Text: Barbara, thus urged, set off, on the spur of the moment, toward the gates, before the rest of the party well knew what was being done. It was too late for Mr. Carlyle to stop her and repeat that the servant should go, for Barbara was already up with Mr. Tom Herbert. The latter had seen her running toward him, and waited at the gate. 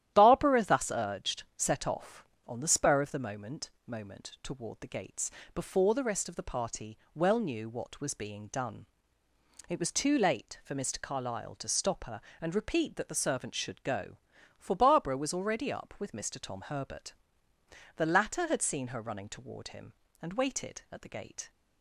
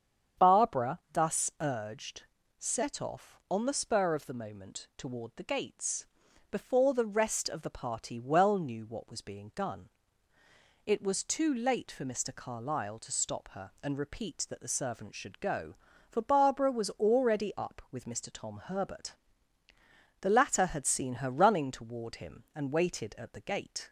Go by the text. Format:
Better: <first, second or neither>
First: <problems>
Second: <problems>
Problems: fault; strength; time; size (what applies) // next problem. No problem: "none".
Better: second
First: starts louder than the rest; strong; until 1.1 s; 12 dB // says "moment" twice; at 3.8 s // pauses between "party" and "well"; slight; at 6.9 s; 0.16 s long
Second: starts louder than the rest; strong; until 1.5 s; 8 dB